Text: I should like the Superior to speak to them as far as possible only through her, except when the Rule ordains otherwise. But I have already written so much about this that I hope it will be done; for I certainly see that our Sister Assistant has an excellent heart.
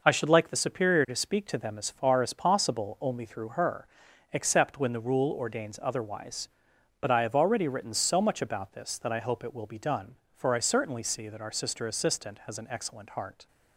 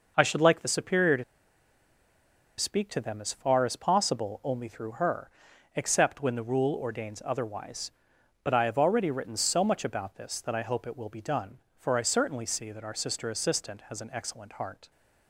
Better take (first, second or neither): first